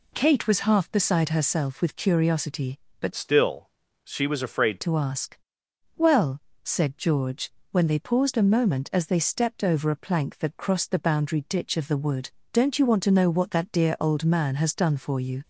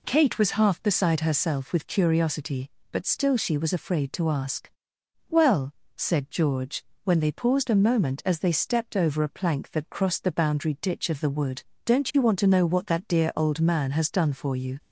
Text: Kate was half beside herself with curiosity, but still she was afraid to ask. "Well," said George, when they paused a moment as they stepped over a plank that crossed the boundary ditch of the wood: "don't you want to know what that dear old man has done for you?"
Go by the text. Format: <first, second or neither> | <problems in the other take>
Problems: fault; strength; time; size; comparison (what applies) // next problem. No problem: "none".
second | changes voice from "still" to "afraid"; from 3.1 to 4.7 s; 1.6 s long // pauses between "still" and "she"; slight; at 3.6 s; 0.34 s long